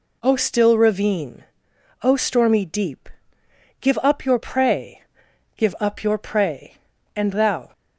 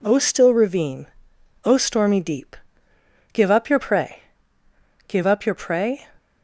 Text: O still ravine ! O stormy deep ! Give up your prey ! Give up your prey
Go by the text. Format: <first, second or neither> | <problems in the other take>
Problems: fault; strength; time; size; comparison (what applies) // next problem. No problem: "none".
second | goes on to say "And thou"; from 7.1 s on; 0.54 s long